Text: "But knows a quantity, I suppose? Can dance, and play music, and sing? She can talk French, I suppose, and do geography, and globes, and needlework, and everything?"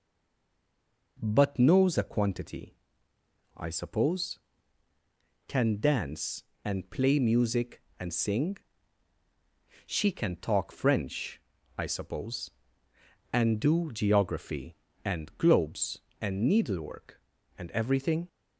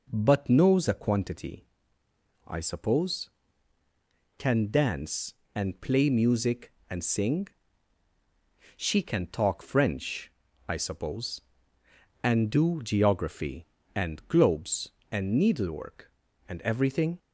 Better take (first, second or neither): second